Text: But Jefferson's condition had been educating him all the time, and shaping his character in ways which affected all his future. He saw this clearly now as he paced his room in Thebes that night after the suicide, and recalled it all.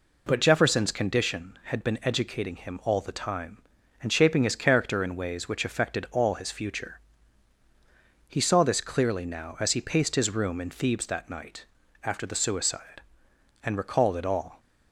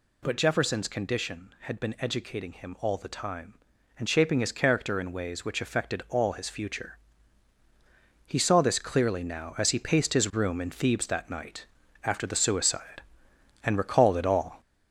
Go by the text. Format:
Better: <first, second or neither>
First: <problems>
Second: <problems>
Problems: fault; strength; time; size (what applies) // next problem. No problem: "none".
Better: first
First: pauses between "night" and "after"; at 11.6 s; 0.38 s long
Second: gets louder; noticeable; throughout; 5 dB // pauses between "night" and "after"; at 11.6 s; 0.38 s long